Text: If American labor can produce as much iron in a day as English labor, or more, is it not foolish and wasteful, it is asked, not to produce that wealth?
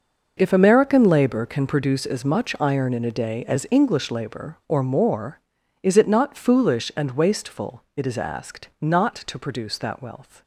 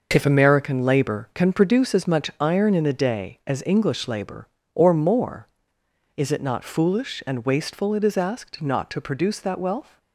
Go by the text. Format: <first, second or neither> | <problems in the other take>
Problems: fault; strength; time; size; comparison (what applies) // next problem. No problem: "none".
neither | none